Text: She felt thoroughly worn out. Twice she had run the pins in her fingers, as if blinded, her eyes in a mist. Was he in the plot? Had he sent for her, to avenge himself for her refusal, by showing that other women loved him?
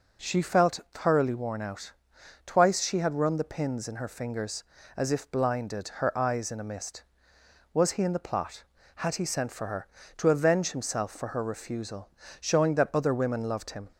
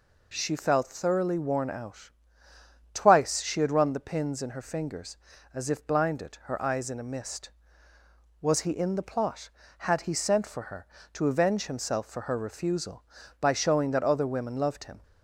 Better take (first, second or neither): second